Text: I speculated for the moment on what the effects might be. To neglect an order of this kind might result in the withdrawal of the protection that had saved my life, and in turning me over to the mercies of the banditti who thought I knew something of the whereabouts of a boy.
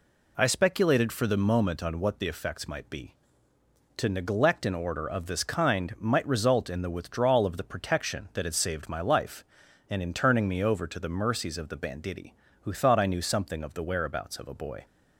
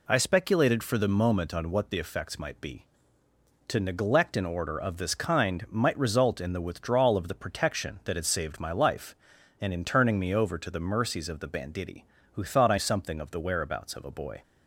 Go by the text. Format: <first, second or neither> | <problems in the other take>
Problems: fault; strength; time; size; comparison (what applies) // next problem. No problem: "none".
first | skips "knew"; at 12.7 s